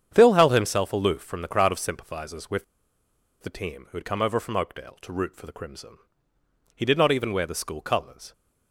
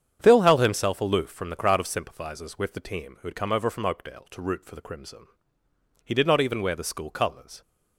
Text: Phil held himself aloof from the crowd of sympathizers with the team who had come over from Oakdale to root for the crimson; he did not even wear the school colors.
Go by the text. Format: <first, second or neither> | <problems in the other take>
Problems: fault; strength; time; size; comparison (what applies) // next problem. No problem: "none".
second | starts louder than the rest; strong; until 1.1 s; 8.5 dB; strong in the second // pauses between "with" and "the"; noticeable; at 2.6 s; 0.77 s long